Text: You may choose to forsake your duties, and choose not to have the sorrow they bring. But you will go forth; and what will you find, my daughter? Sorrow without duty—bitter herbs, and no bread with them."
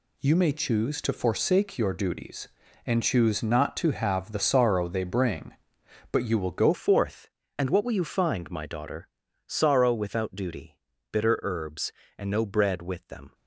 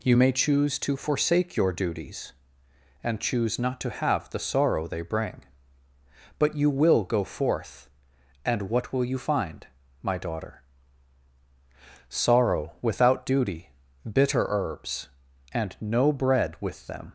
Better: second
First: changes voice at "forth"; from 6.7 s on; 6.6 s long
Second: none

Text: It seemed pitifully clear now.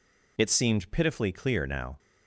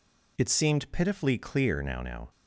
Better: first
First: none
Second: says "now" twice; at 2.0 s

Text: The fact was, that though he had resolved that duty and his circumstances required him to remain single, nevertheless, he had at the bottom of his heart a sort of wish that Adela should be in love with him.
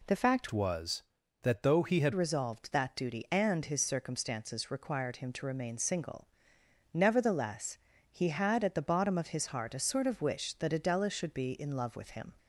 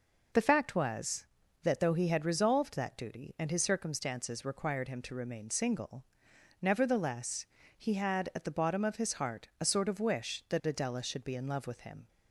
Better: second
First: changes voice from "was" to "had"; from 0.5 to 2.1 s; 1.6 s long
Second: none

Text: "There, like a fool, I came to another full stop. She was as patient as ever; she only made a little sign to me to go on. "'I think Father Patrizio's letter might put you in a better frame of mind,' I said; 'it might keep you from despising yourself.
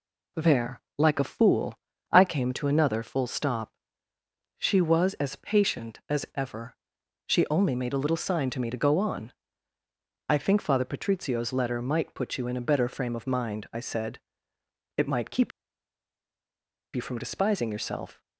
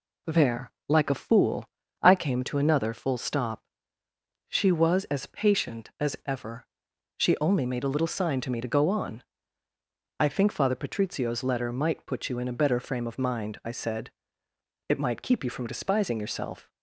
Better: second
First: pauses between "keep" and "you"; strong; at 15.5 s; 1.4 s long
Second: none

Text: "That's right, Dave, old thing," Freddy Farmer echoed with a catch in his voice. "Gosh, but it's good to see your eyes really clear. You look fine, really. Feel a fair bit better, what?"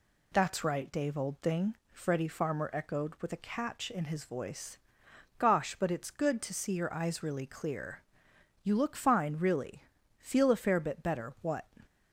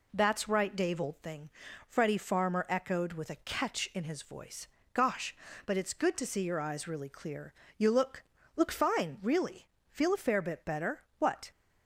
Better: first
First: none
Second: says "look" twice; at 8.5 s

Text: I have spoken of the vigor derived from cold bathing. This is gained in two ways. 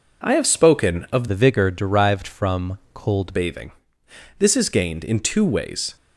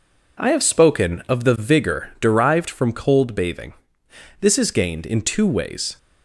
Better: second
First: changes voice from "the" to "cold"; from 1.2 to 3.3 s; 2.1 s long // pauses between "from" and "cold"; slight; at 2.7 s; 0.16 s long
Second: none

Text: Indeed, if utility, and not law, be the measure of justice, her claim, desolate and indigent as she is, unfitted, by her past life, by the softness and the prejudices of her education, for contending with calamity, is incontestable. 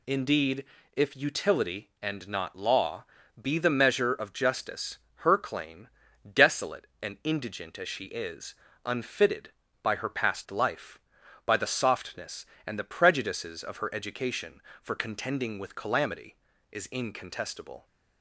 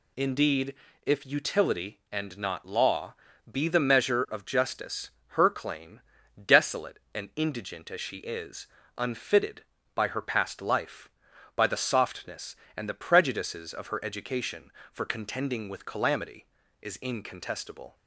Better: neither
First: none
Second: none

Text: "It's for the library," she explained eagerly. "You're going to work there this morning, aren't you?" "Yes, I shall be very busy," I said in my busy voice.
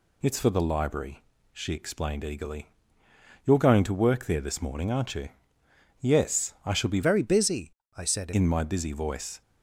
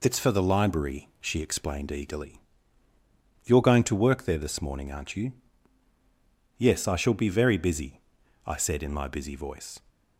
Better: second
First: changes voice from "very" to "said"; from 7.0 to 8.3 s; 1.3 s long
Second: none

